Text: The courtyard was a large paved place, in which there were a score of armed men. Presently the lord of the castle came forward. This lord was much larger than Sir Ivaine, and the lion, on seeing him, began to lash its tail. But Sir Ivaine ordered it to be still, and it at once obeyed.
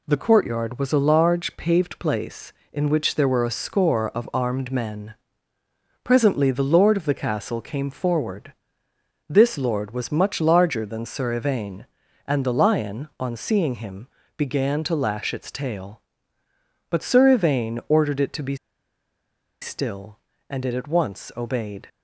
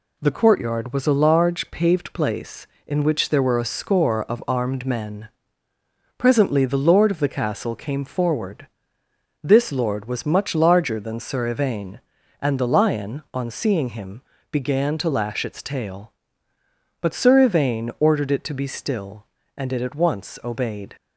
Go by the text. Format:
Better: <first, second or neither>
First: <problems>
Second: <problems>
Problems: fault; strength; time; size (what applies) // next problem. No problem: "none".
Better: second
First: pauses between "be" and "still"; at 18.5 s; 1.0 s long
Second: none